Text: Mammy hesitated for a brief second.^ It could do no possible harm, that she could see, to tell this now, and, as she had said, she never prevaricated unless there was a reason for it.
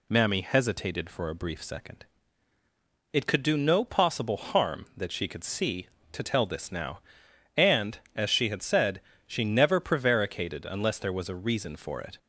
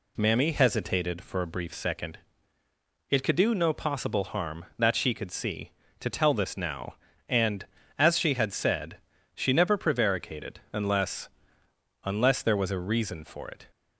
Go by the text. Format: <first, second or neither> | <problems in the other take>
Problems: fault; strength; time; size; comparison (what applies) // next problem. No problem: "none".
first | says "unless" twice; at 12.0 s